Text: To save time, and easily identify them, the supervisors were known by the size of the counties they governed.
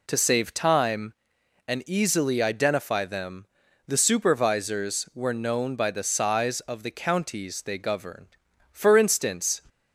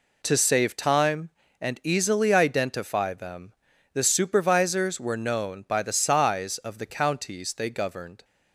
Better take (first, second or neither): second